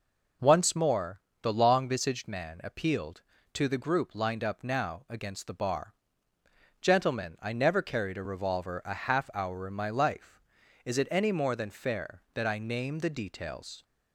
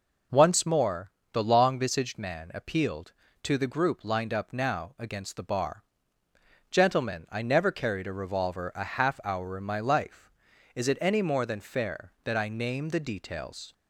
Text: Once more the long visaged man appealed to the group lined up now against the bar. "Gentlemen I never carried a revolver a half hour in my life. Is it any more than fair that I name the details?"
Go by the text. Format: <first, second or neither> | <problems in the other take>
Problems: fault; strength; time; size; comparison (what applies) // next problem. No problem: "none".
neither | pauses between "more" and "the"; slight; the same in both